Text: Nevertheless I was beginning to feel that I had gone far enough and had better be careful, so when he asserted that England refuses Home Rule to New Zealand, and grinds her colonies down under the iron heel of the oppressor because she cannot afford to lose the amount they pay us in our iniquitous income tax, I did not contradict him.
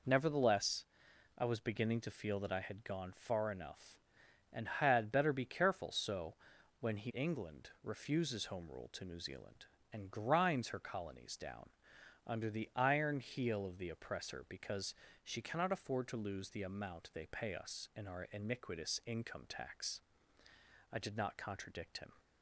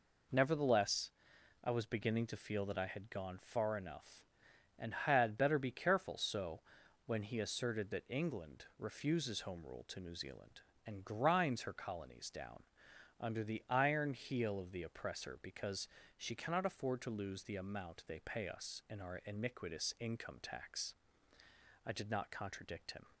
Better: second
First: pauses between "Nevertheless" and "I"; noticeable; at 0.8 s; 0.52 s long // pauses between "so" and "when"; noticeable; at 6.3 s; 0.46 s long // skips "asserted that"; at 7.1 s // pauses between "down" and "under"; noticeable; at 11.6 s; 0.56 s long // pauses between "because" and "she"; slight; at 14.9 s; 0.30 s long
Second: pauses between "Nevertheless" and "I"; noticeable; at 1.1 s; 0.52 s long // pauses between "so" and "when"; noticeable; at 6.6 s; 0.46 s long // pauses between "down" and "under"; noticeable; at 12.6 s; 0.56 s long // pauses between "because" and "she"; slight; at 15.8 s; 0.30 s long

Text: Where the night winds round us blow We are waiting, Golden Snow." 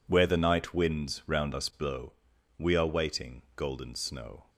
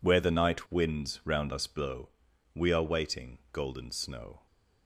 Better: neither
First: pauses between "blow" and "We"; at 2.1 s; 0.44 s long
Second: pauses between "blow" and "We"; at 2.0 s; 0.44 s long

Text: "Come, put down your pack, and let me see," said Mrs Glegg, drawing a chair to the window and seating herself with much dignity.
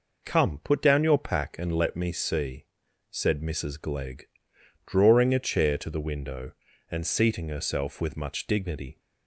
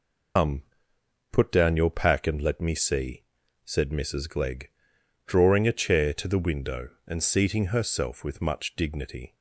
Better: first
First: none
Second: loses the start of "Come"; at 0.3 s; 125 ms

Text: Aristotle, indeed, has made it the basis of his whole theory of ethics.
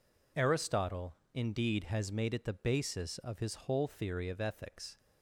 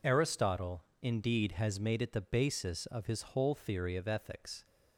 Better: neither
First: none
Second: none

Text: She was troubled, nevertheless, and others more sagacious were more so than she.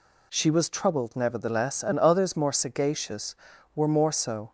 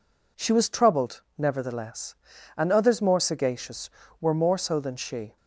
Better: second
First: stops before "than she"; at 4.4 s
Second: none

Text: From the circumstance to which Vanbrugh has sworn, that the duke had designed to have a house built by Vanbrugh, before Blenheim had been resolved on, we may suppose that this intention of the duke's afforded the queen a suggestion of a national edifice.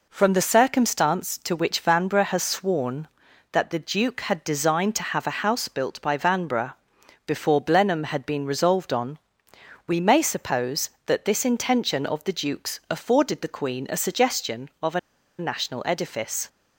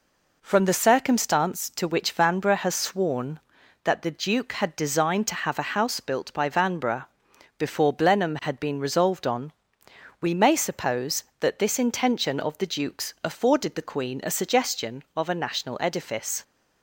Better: second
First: pauses between "a" and "national"; at 14.9 s; 0.40 s long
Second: none

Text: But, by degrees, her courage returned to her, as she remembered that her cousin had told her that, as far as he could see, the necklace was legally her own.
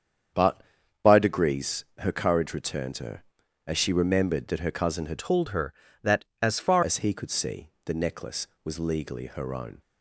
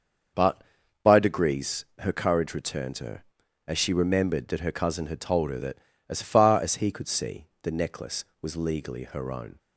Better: second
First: starts louder than the rest; strong; until 1.7 s; 7.5 dB // changes voice from "told" to "far"; from 5.1 to 6.8 s; 1.7 s long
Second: starts louder than the rest; until 1.7 s; 6 dB

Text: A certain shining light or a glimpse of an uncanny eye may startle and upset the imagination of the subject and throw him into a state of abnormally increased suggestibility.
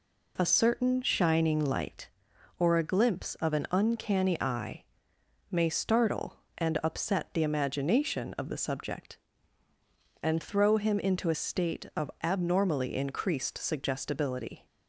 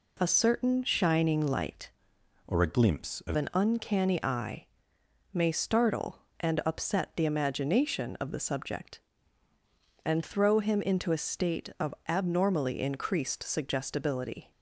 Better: first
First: pauses between "eye" and "may"; noticeable; at 4.8 s; 0.66 s long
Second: changes voice from "or" to "of"; from 2.4 to 3.3 s; 0.9 s long // pauses between "eye" and "may"; noticeable; at 4.6 s; 0.66 s long

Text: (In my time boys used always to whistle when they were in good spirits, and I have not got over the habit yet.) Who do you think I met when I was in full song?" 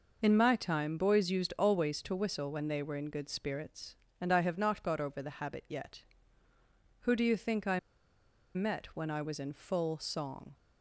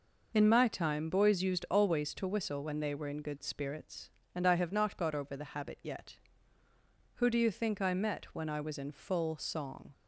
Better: second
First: pauses between "I" and "met"; noticeable; at 7.7 s; 0.76 s long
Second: none

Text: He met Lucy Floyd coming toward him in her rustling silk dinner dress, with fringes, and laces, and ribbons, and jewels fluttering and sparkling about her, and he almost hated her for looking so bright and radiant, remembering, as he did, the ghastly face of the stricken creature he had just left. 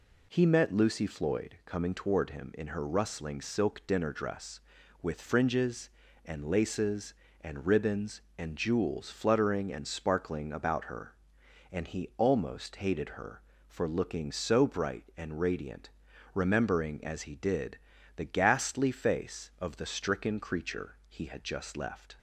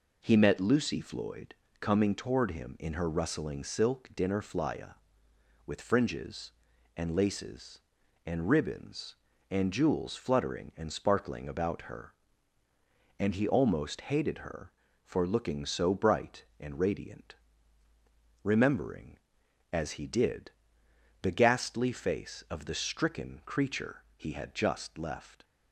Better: first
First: none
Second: pauses between "Floyd" and "coming"; slight; at 1.5 s; 0.28 s long // says "flya" for "dress"; at 4.4 s // pauses between "creature" and "he"; slight; at 24.0 s; 0.16 s long

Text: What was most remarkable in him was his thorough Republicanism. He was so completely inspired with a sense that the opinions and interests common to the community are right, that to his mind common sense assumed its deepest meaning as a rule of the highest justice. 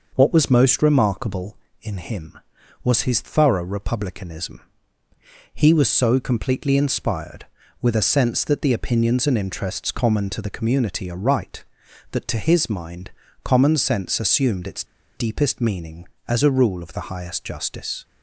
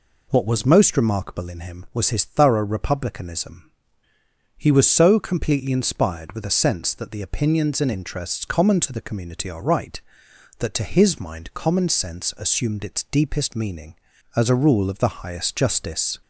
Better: second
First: pauses between "mind" and "common"; slight; at 13.0 s; 0.32 s long // pauses between "its" and "deepest"; slight; at 14.8 s; 0.32 s long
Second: none

